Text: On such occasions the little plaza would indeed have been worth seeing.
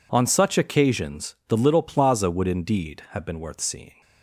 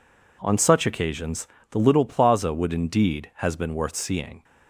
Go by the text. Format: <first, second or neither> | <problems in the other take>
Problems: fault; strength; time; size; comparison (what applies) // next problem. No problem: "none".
first | pauses between "occasions" and "the"; slight; at 1.4 s; 0.24 s long // says "has" for "have"; at 3.3 s